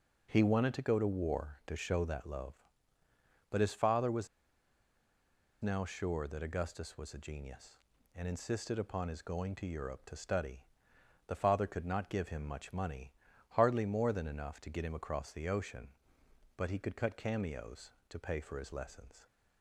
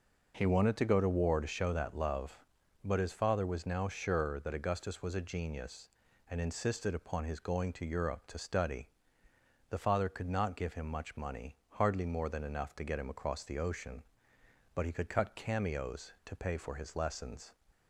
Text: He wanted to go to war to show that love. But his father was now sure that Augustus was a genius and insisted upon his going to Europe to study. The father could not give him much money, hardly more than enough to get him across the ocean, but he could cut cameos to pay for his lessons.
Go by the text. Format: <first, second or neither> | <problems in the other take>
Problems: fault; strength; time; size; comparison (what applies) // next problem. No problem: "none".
second | pauses between "was" and "now"; strong; at 4.2 s; 1.3 s long